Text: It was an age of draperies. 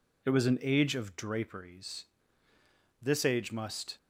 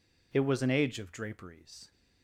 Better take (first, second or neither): second